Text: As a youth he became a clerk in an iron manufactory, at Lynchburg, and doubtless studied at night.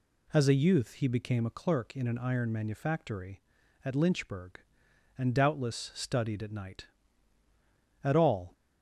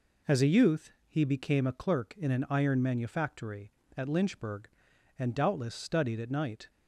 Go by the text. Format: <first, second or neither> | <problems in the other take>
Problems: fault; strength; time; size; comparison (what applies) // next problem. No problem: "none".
second | goes on to say "At all"; slight; from 8.0 s on; 0.48 s long